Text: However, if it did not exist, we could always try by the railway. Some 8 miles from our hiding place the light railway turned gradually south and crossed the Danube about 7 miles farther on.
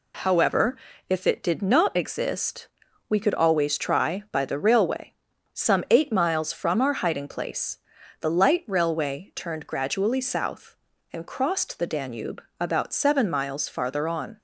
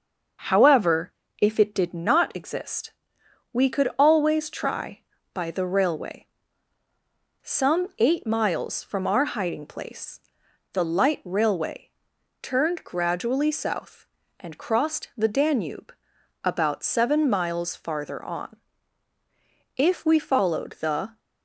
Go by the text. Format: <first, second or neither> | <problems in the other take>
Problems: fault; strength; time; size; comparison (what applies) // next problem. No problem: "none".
first | starts louder than the rest; until 1.7 s; 6.5 dB // pauses between "place" and "the"; noticeable; at 10.1 s; 0.52 s long; also in the first // pauses between "railway" and "turned"; noticeable; at 11.8 s; 0.52 s long // pauses between "Danube" and "about"; noticeable; at 15.9 s; 0.50 s long; slight in the first // goes on to say "If we followed the"; from 19.7 s on; 1.4 s long